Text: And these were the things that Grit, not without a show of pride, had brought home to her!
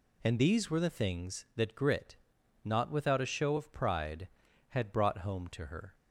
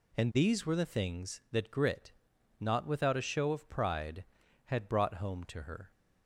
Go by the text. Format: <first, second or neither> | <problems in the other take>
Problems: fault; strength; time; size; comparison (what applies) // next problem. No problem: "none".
neither | none